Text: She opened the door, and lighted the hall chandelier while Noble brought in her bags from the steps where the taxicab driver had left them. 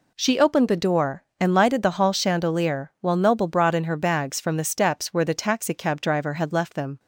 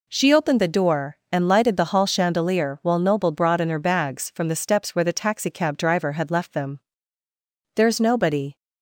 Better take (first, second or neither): first